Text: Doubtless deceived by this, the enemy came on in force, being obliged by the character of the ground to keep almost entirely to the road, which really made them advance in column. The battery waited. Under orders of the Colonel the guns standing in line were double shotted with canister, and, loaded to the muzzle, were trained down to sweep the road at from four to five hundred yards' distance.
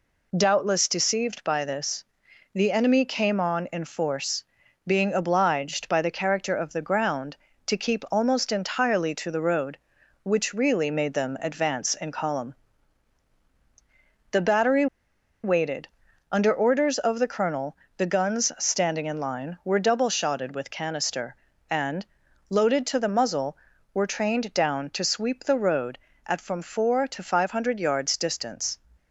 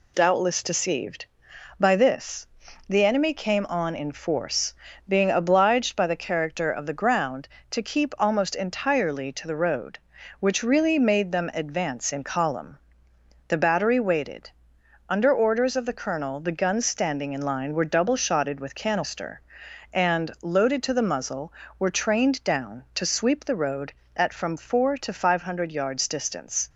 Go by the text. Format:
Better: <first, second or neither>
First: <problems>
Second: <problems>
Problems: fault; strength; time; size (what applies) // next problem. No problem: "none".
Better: second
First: pauses between "battery" and "waited"; noticeable; at 14.8 s; 0.58 s long // pauses between "Colonel" and "the"; slight; at 17.7 s; 0.22 s long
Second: none